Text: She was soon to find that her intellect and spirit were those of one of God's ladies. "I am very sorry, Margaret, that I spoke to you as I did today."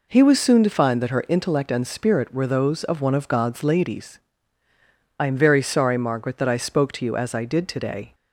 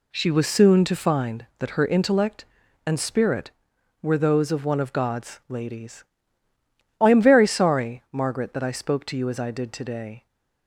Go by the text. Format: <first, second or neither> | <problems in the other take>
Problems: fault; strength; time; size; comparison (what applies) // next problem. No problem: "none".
second | says "He" for "She"; at 0.1 s